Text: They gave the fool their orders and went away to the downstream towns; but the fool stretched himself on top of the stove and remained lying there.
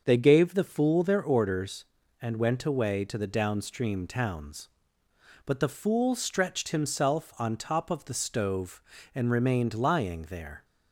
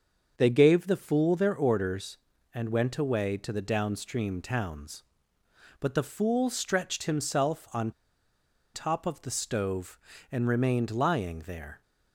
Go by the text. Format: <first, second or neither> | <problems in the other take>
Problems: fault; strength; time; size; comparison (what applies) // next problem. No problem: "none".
first | starts louder than the rest; until 1.3 s; 6.5 dB; also in the first // pauses between "on" and "top"; noticeable; at 7.9 s; 0.83 s long